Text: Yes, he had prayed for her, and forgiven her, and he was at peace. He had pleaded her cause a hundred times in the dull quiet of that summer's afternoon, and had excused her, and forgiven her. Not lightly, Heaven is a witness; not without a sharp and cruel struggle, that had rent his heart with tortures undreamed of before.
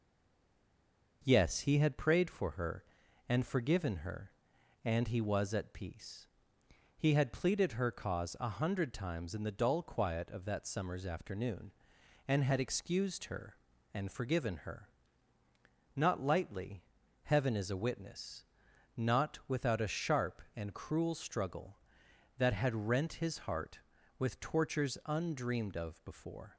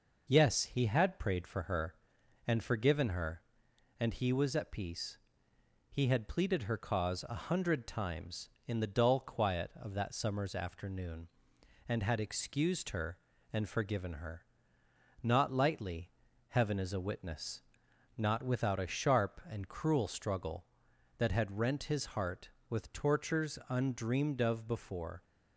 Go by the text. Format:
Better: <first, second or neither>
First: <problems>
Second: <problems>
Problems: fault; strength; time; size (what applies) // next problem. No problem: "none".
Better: second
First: stays silent before the first word; noticeable; until 1.2 s; 1.2 s long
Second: none